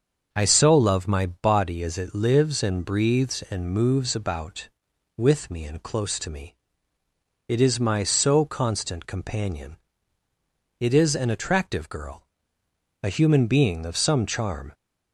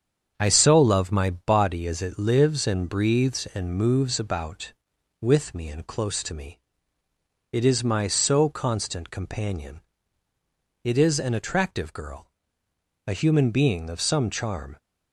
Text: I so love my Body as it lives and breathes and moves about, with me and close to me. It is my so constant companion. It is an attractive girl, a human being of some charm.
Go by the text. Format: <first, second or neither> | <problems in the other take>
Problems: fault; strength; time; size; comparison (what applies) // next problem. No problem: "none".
first | gets quieter; noticeable; throughout; 4 dB // starts louder than the rest; strong; until 1.3 s; 7.5 dB; also in the first